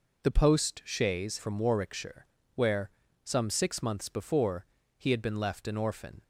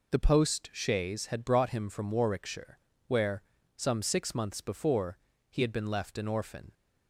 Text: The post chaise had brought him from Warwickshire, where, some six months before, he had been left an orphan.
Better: second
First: skips "had brought him"; at 1.3 s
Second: none

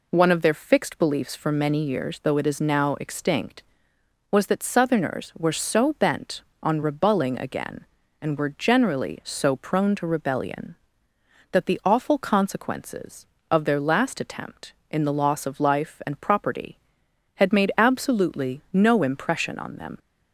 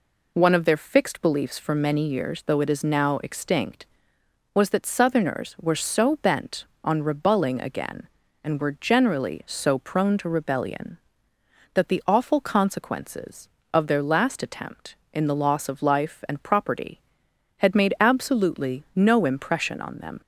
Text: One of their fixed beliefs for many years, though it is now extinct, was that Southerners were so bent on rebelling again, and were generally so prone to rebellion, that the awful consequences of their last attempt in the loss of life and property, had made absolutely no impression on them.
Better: neither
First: none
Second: none

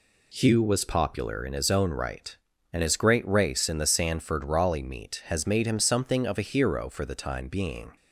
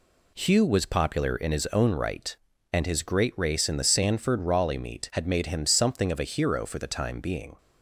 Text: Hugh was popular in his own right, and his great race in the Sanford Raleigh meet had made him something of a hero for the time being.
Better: second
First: says "has" for "had"; at 5.2 s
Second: none

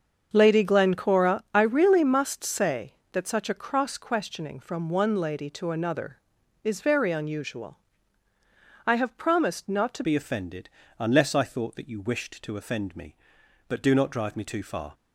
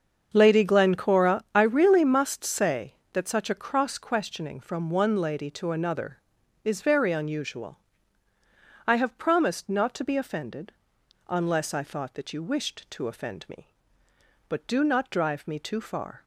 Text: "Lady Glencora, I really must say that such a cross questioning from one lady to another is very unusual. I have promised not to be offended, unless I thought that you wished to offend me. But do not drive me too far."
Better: second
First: starts louder than the rest; until 1.3 s; 6.5 dB // changes voice at "be"; from 10.0 s on; 4.9 s long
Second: starts louder than the rest; until 1.3 s; 6.5 dB

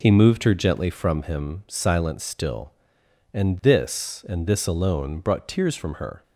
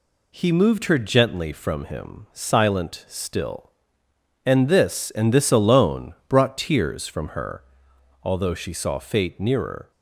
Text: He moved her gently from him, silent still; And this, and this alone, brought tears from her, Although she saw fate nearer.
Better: second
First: stops before "Although she saw fate nearer"; at 6.2 s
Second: none

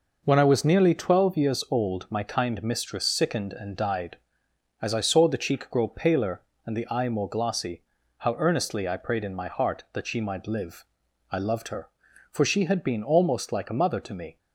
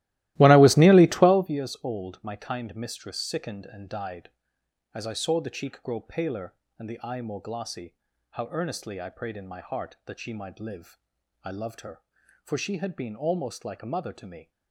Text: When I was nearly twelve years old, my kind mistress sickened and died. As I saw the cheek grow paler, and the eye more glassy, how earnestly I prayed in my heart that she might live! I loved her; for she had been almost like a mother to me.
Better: first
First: none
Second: starts louder than the rest; strong; until 1.6 s; 16.5 dB

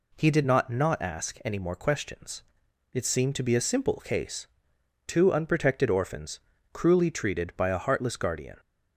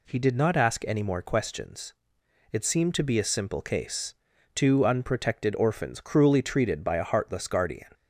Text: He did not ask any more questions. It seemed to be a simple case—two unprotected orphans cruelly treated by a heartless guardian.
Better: second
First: says "not" twice; at 0.6 s // pauses between "orphans" and "cruelly"; slight; at 6.3 s; 0.32 s long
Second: none

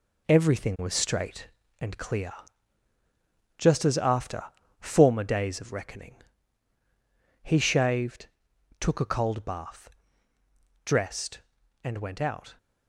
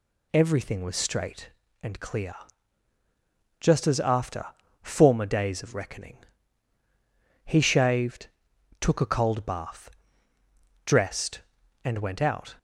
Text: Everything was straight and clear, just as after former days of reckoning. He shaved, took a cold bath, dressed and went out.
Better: second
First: gets quieter; throughout; 7 dB // pauses between "after" and "former"; at 4.4 s; 0.38 s long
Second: pauses between "after" and "former"; at 4.4 s; 0.38 s long

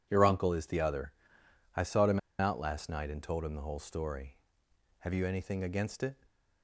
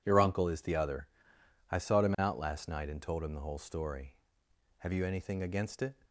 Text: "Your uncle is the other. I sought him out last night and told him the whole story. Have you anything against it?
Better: second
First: pauses between "him" and "out"; slight; at 2.1 s; 0.19 s long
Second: none

